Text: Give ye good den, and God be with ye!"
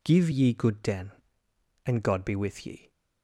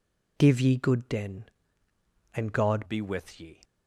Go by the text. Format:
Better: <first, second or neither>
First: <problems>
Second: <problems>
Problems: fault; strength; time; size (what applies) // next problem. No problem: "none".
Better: first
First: none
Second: changes voice at "be"; from 2.8 s on; 0.8 s long